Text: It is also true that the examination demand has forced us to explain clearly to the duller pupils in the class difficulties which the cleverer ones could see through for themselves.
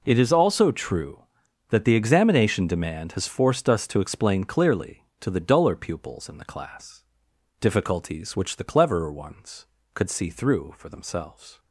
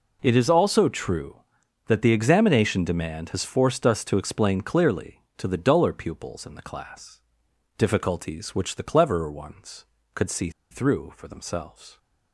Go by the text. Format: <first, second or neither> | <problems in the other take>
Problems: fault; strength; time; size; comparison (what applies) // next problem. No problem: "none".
first | pauses between "class" and "difficulties"; noticeable; at 7.2 s; 0.56 s long; noticeable in the first // pauses between "see" and "through"; slight; at 10.4 s; 0.21 s long